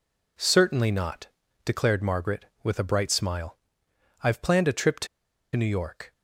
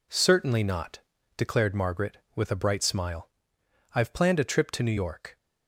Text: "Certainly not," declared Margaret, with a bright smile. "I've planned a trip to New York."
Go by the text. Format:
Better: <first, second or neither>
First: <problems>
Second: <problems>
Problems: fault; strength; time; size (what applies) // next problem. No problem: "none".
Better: second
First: pauses between "to" and "New"; noticeable; at 5.0 s; 0.48 s long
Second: none